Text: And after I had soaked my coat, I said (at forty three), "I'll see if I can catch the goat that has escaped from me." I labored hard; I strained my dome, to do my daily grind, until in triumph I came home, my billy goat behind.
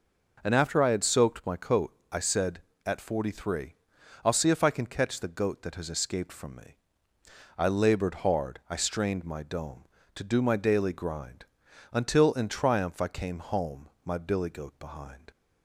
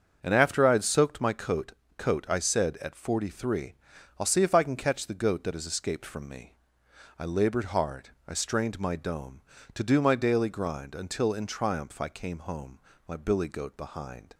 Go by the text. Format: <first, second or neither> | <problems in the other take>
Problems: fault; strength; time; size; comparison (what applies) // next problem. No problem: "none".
first | starts louder than the rest; until 1.2 s; 6.5 dB // says "coat" twice; at 1.9 s